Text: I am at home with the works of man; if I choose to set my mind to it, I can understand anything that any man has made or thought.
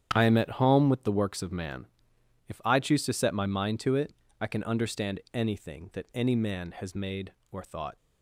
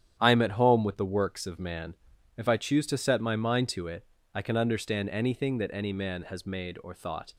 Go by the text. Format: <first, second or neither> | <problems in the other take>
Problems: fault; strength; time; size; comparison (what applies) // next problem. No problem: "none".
neither | starts louder than the rest; strong; the same in both